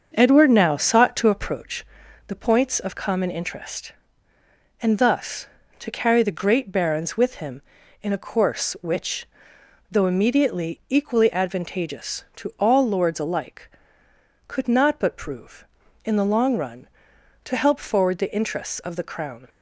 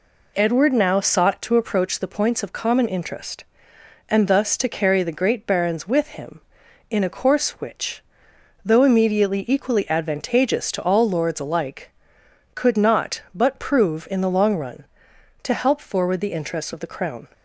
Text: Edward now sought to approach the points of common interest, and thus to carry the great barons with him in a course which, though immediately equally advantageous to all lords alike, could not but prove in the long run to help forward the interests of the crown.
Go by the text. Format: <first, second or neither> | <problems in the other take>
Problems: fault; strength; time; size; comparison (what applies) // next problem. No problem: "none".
second | starts louder than the rest; until 1.6 s; 6.5 dB // pauses between "approach" and "the"; at 1.8 s; 0.40 s long